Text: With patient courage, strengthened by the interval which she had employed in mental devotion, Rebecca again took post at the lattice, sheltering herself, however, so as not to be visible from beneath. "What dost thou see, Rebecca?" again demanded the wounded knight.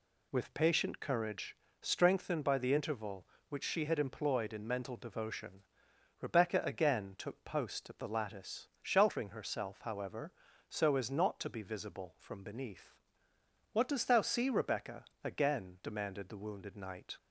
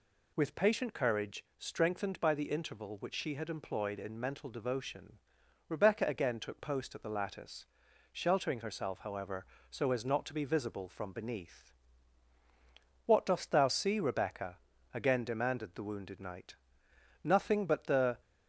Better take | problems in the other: first | goes on to say "Nothing but the"; noticeable; from 17.2 s on; 0.95 s long

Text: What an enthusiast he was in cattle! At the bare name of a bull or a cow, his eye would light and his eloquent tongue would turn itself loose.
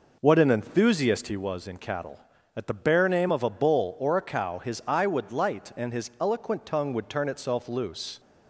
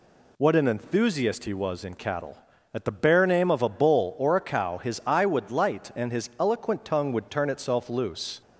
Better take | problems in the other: second | starts louder than the rest; noticeable; until 1.4 s; 5 dB

